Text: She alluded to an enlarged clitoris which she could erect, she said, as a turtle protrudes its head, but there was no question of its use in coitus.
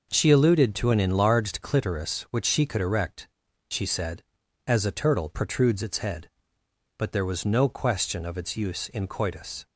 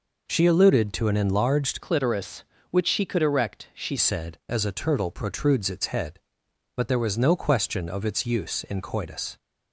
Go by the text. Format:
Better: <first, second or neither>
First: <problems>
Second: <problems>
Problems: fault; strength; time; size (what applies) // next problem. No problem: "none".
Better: first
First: none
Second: changes voice from "clitoris" to "she"; from 1.8 to 3.9 s; 2.1 s long